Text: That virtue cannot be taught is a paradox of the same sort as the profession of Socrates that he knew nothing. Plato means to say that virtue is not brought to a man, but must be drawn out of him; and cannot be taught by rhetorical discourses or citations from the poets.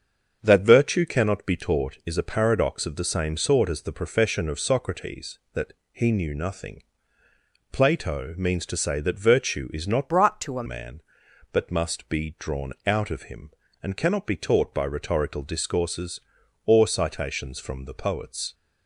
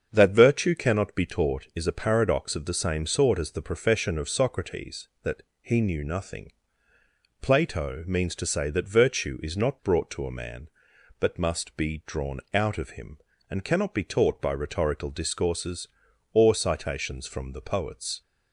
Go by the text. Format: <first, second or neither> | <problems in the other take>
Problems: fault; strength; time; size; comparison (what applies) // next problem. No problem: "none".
second | starts louder than the rest; until 1.4 s; 7 dB; also in the second // pauses between "that" and "he"; slight; at 5.7 s; 0.18 s long; slight in the second // changes voice from "brought" to "a"; from 10.0 to 10.6 s; 0.6 s long